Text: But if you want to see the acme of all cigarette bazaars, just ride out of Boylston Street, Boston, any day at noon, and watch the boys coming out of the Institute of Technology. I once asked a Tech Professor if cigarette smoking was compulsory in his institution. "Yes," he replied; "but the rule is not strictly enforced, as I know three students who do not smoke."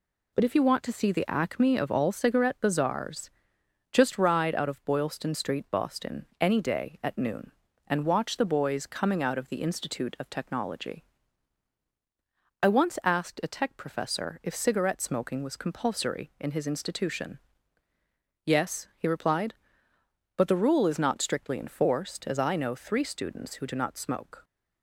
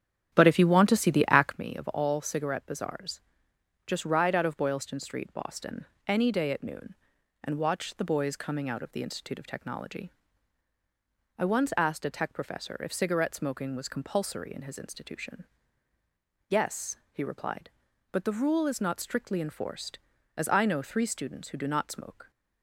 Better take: first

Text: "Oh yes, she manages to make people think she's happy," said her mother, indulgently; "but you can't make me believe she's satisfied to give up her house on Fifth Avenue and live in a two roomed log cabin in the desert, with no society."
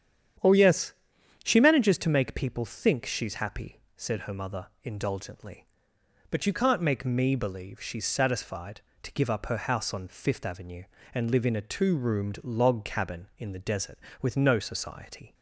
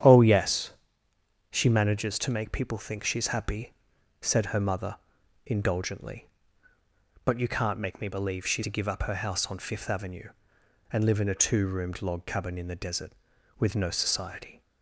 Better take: first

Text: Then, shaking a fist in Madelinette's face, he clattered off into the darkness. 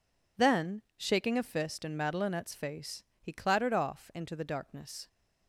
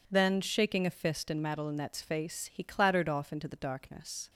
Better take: neither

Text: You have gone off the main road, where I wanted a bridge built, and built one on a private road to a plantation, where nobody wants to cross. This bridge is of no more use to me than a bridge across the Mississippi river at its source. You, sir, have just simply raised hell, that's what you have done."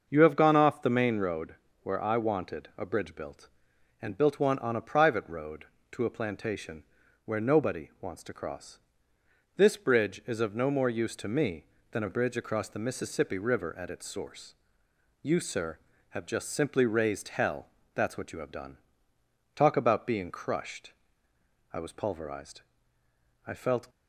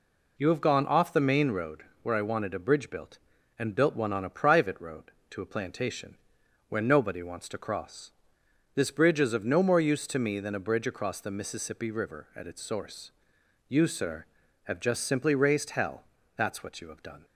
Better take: second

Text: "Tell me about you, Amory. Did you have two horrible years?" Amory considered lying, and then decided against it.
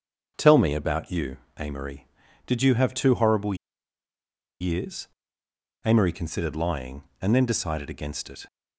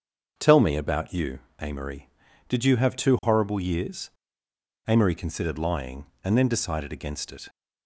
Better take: second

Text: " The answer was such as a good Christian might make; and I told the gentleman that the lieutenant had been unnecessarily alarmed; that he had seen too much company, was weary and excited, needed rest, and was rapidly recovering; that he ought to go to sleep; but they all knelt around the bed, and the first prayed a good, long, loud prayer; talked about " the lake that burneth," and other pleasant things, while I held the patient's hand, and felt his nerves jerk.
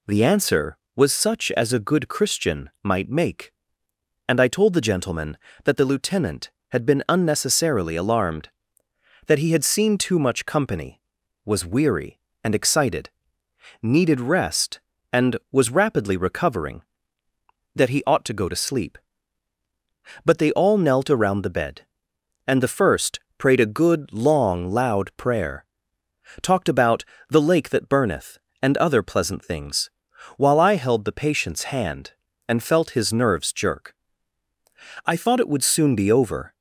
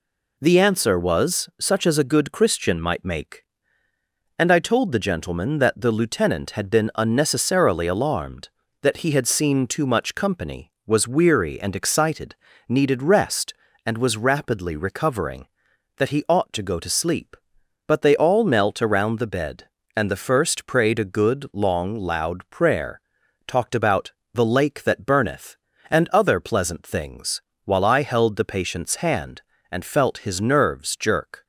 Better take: second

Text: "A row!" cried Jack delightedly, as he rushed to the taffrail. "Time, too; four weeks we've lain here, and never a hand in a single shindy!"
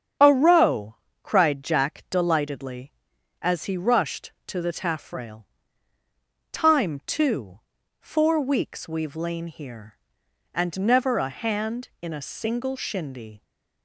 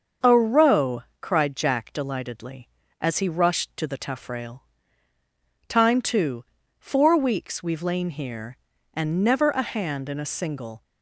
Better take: first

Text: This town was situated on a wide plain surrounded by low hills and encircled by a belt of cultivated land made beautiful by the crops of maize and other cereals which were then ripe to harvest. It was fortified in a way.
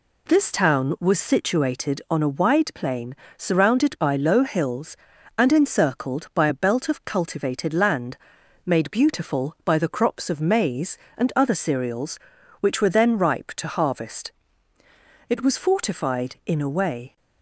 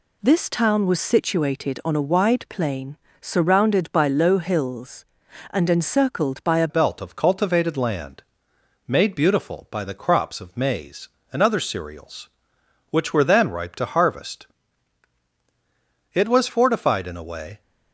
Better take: first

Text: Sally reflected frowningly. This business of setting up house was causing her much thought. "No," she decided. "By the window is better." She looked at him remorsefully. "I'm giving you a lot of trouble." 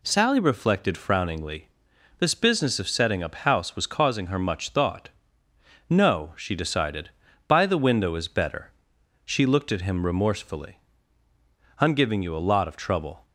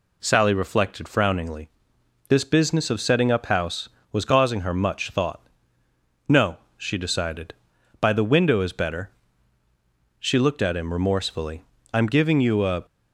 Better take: first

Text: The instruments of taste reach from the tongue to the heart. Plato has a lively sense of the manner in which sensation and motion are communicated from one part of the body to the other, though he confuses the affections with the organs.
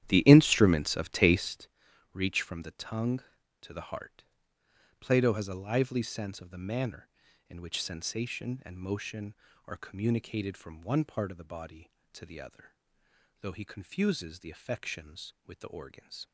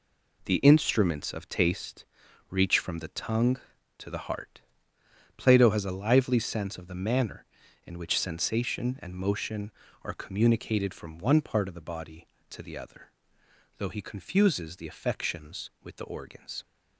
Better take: second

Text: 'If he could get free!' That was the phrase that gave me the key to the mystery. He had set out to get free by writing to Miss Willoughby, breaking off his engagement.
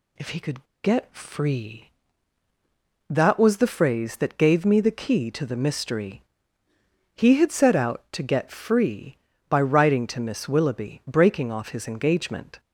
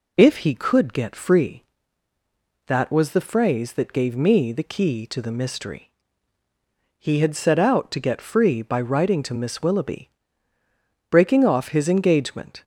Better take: second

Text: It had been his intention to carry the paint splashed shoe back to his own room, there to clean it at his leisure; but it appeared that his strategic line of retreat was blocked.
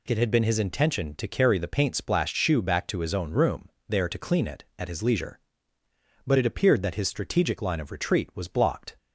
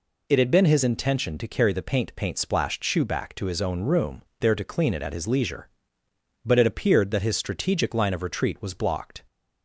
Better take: first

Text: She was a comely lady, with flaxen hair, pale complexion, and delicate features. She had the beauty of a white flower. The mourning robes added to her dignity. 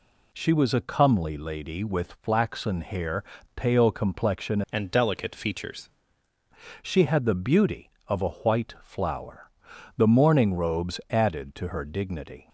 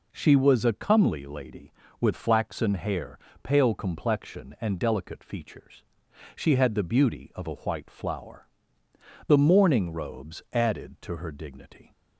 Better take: second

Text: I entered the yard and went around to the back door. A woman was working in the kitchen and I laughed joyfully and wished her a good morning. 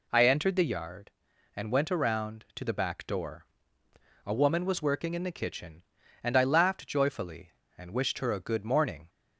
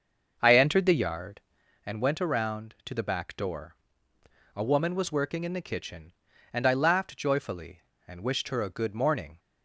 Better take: first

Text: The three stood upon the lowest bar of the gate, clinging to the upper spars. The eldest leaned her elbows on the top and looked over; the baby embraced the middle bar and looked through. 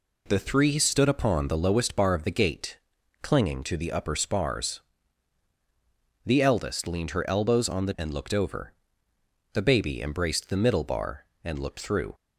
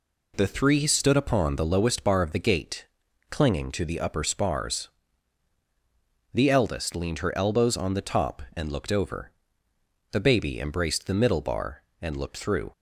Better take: second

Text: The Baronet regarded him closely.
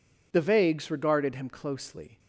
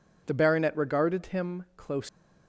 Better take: second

